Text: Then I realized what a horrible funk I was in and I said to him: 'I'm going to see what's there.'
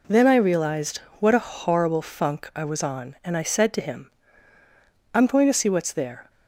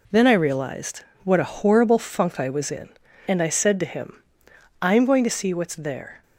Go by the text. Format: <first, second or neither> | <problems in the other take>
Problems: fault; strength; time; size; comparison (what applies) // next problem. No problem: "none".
second | pauses between "realized" and "what"; slight; at 0.9 s; 0.18 s long; slight in the second // says "on" for "in"; at 2.8 s